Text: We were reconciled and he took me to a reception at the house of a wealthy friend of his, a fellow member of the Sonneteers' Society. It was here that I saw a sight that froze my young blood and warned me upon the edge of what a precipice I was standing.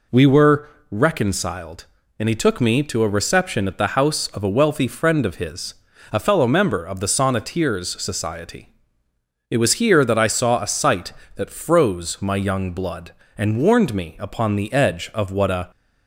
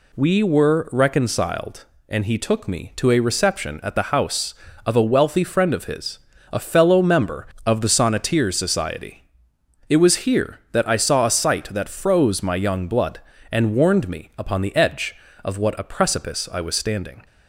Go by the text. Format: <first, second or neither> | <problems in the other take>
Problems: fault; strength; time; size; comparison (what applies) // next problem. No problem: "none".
second | pauses between "were" and "reconciled"; slight; at 0.6 s; 0.24 s long // stops before "precipice I was standing"; at 15.7 s